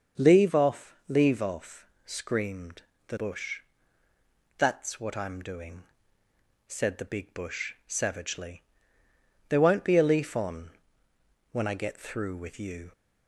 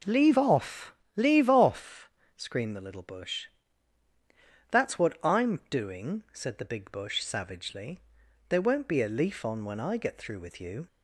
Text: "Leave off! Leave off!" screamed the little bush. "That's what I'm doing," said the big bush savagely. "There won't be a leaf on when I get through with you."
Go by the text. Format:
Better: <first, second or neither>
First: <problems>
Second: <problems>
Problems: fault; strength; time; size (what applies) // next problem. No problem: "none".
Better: second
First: starts louder than the rest; until 1.3 s; 6.5 dB // pauses between "screamed" and "the"; slight; at 2.8 s; 0.24 s long // skips "little"; at 3.1 s // pauses between "on" and "when"; noticeable; at 10.7 s; 0.80 s long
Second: none